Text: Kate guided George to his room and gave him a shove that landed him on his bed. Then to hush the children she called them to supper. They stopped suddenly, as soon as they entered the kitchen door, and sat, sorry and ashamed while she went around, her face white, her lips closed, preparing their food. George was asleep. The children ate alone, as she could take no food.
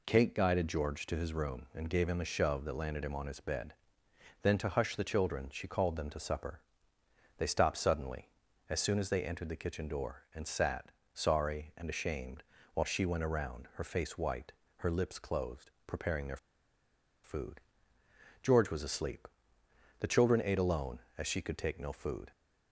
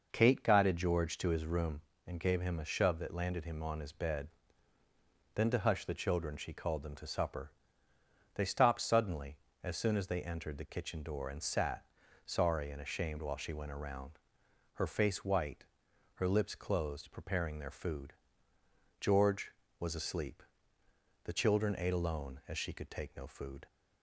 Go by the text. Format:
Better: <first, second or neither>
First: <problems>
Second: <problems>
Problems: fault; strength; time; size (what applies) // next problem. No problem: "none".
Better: second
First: pauses between "ashamed" and "while"; slight; at 12.4 s; 0.32 s long // pauses between "their" and "food"; noticeable; at 16.3 s; 0.87 s long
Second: none